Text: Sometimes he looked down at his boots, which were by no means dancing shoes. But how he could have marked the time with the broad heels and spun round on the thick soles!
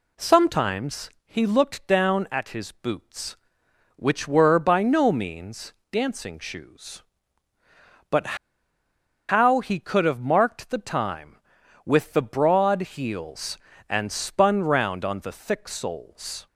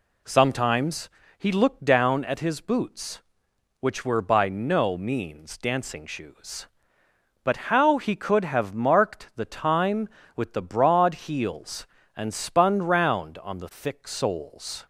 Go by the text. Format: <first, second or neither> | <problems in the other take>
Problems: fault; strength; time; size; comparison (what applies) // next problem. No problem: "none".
second | pauses between "Sometimes" and "he"; slight; at 1.0 s; 0.16 s long; slight in the second // pauses between "means" and "dancing"; slight; at 5.7 s; 0.18 s long // pauses between "But" and "how"; noticeable; at 8.3 s; 0.93 s long